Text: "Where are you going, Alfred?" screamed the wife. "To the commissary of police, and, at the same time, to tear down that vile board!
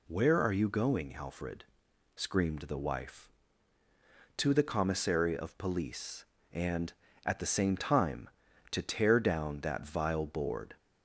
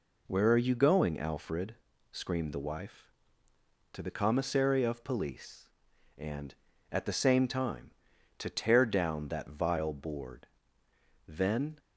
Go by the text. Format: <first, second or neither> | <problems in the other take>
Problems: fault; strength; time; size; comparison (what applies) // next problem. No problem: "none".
first | goes on to say "Then"; from 11.2 s on; 0.50 s long